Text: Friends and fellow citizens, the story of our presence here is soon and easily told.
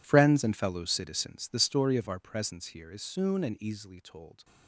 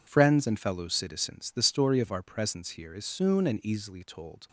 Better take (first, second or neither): second